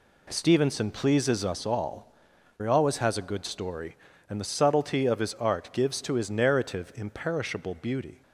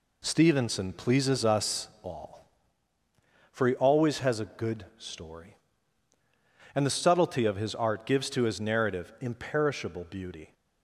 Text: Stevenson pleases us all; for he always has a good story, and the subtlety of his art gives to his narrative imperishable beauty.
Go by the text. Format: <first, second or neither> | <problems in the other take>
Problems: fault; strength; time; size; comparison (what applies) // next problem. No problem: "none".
second | skips "for"; at 2.3 s